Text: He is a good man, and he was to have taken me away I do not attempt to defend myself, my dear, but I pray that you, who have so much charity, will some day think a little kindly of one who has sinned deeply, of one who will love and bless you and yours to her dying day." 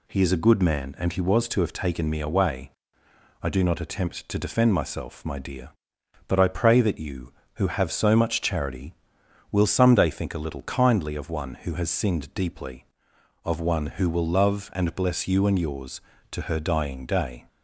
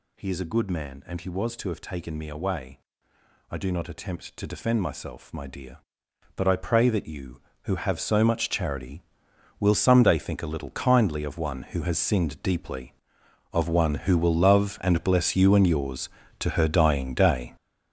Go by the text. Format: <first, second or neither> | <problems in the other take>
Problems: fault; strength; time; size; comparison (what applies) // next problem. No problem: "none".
first | gets louder; strong; throughout; 9.5 dB // pauses between "away" and "I"; noticeable; at 2.7 s; 0.72 s long; noticeable in the first